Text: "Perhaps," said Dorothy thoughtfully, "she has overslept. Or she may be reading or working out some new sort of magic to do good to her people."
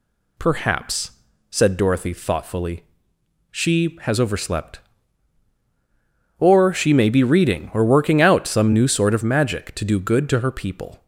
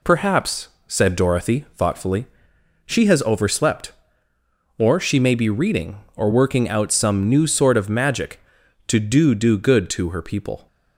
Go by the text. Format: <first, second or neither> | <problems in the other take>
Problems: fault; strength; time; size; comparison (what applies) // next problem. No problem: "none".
first | says "do" twice; at 9.3 s